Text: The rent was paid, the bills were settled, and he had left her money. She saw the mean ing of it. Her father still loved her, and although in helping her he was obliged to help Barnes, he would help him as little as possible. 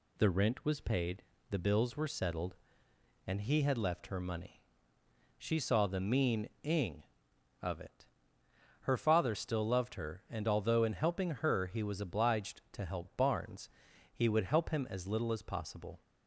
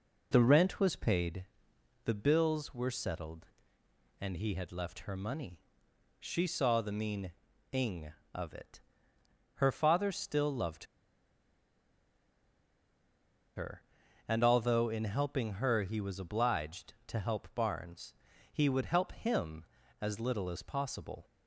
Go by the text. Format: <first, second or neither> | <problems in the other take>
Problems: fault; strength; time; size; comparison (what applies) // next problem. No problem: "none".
first | pauses between "mean" and "ing"; at 7.3 s; 0.38 s long // pauses between "loved" and "her"; strong; at 10.8 s; 2.7 s long